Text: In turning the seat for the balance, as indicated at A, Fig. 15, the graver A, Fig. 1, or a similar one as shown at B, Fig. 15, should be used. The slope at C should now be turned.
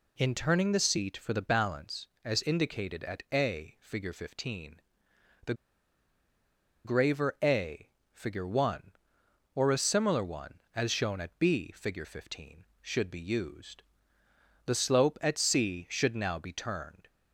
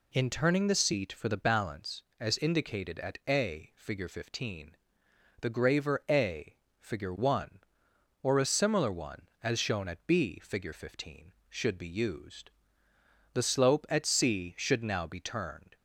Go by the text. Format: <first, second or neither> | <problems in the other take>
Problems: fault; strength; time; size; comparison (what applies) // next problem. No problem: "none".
second | pauses between "the" and "graver"; strong; at 5.5 s; 1.3 s long